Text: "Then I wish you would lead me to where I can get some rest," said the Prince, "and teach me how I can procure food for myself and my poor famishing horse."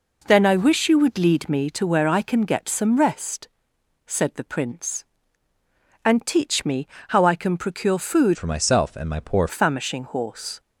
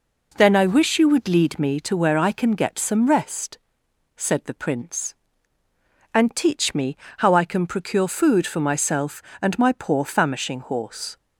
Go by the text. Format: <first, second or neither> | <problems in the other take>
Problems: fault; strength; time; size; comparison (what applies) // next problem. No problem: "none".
second | pauses between "me" and "how"; slight; at 6.8 s; 0.22 s long; slight in the second // changes voice from "for" to "poor"; from 8.3 to 9.4 s; 1.1 s long